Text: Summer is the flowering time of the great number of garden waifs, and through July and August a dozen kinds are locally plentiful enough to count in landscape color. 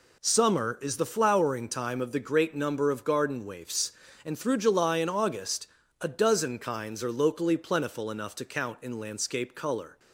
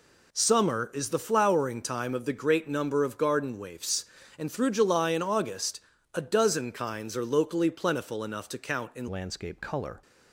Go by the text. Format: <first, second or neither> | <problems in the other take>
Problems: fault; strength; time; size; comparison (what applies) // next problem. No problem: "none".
first | pauses between "August" and "a"; slight; at 5.8 s; 0.34 s long; slight in the first // changes voice at "landscape"; from 9.0 s on; 1.0 s long